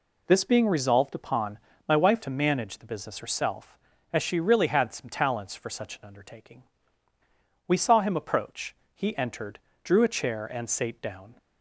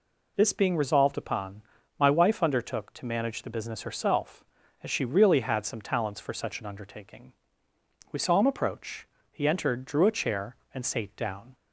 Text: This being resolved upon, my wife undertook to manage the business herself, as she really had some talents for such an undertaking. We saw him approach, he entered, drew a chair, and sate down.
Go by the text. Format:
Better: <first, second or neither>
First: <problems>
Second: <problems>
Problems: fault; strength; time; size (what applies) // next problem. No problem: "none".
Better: second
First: skips "undertook"; at 2.2 s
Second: none